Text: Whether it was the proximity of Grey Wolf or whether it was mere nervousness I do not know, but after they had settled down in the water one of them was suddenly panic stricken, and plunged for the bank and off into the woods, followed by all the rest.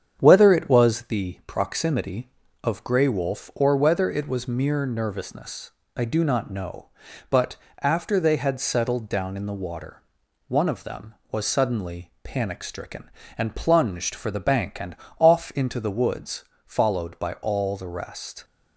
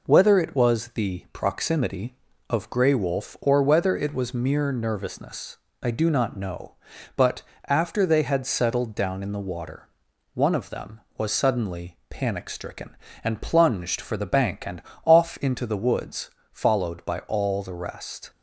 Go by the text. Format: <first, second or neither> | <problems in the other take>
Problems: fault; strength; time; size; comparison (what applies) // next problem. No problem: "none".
second | starts louder than the rest; strong; until 1.1 s; 8 dB // pauses between "nervousness" and "I"; slight; at 5.7 s; 0.24 s long; slight in the second // pauses between "but" and "after"; slight; at 7.5 s; 0.28 s long; slight in the second // pauses between "water" and "one"; noticeable; at 10.0 s; 0.46 s long; noticeable in the second // pauses between "and" and "off"; slight; at 14.9 s; 0.22 s long; slight in the second